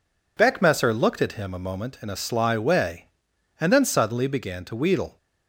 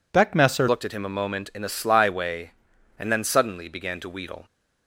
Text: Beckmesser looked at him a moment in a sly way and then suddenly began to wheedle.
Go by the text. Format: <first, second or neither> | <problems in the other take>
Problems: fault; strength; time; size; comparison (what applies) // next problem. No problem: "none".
first | changes voice at "looked"; from 0.6 s on; 3.8 s long